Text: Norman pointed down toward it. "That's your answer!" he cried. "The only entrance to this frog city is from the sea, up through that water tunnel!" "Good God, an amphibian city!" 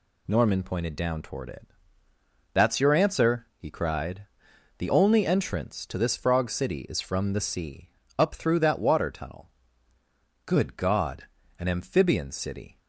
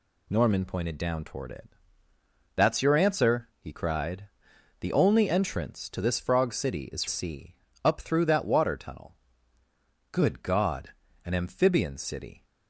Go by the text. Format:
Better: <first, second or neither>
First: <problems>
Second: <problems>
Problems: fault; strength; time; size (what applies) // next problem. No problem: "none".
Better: first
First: none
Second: skips "from the"; at 7.0 s